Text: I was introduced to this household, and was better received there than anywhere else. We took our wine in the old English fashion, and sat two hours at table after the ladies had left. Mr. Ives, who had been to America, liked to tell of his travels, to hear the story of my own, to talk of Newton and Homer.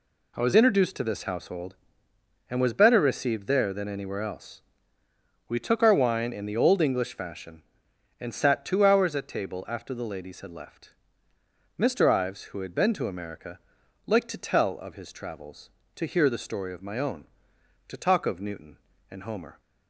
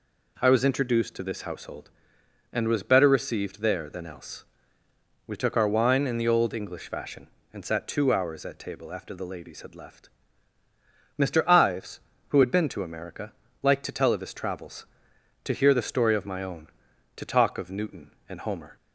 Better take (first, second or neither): first